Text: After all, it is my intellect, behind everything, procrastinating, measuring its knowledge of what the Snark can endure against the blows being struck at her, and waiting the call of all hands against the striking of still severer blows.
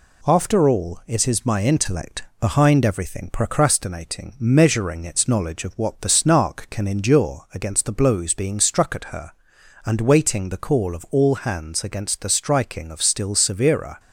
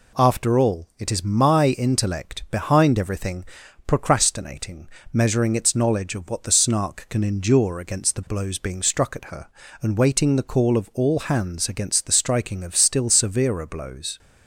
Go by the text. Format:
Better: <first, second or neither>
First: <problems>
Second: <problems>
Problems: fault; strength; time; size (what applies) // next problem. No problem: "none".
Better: second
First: stops before "blows"; at 13.9 s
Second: none